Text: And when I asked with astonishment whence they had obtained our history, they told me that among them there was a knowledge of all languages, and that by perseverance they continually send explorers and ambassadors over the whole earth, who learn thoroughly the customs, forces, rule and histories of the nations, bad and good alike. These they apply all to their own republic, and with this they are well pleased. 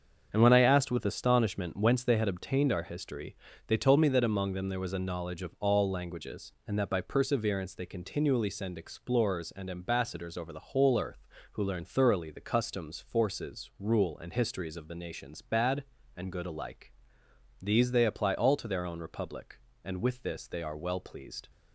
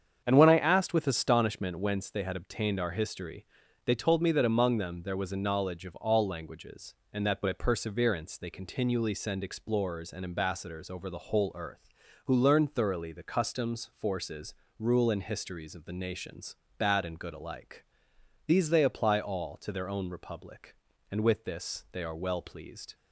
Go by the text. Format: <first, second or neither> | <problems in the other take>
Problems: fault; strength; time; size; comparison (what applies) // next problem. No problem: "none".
neither | starts louder than the rest; the same in both